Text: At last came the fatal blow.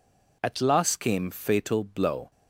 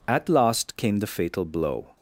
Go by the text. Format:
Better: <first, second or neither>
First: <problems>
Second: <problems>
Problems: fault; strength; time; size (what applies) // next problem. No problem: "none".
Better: second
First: skips "the"; at 1.3 s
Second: none